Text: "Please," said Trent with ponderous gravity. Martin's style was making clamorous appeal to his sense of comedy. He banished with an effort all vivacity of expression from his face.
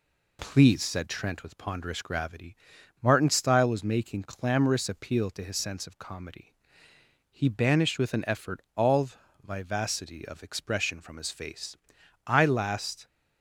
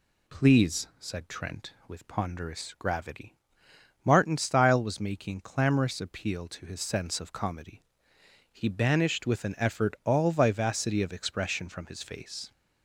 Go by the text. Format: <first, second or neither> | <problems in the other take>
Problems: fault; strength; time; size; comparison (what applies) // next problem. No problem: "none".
second | pauses between "all" and "vivacity"; slight; at 9.1 s; 0.36 s long // goes on to say "I last"; noticeable; from 12.2 s on; 0.80 s long